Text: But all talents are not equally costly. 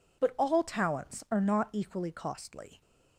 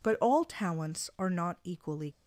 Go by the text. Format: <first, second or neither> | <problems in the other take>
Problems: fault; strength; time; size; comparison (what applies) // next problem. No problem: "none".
first | stops before "costly"; at 2.1 s